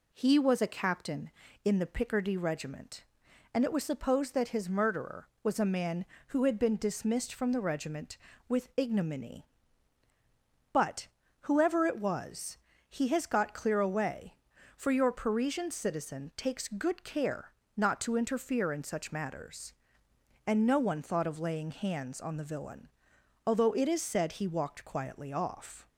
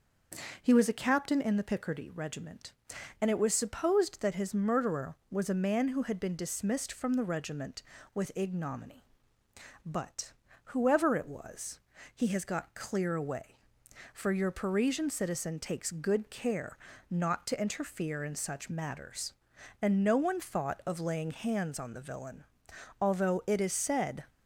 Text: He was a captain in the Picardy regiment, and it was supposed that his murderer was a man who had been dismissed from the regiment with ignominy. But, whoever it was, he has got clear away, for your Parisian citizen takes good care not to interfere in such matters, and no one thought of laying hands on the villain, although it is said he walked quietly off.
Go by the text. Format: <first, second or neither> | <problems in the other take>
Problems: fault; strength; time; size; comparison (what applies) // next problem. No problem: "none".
first | starts louder than the rest; noticeable; until 1.6 s; 6 dB // pauses between "care" and "not"; slight; at 16.7 s; 0.34 s long; slight in the first // stops before "he walked quietly off"; at 24.2 s